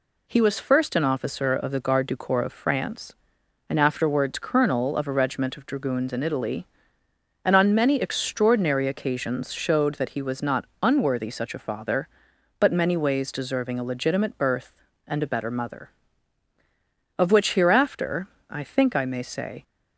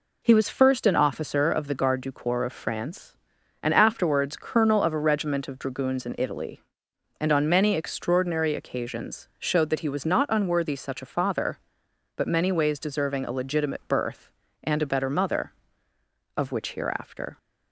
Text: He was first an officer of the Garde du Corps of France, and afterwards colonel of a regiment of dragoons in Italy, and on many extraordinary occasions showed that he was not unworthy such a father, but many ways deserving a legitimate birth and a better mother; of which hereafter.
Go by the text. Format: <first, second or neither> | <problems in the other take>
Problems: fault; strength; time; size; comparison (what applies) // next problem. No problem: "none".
second | pauses between "not" and "unworthy"; slight; at 10.6 s; 0.18 s long // goes on to say "I think I may say"; noticeable; from 18.4 s on; 1.1 s long